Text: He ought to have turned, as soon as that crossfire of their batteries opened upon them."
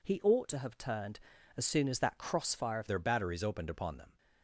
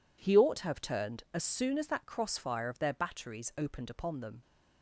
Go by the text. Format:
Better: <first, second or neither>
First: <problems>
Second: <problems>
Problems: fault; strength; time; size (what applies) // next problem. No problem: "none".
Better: second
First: changes voice at "their"; from 2.8 s on; 1.3 s long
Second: none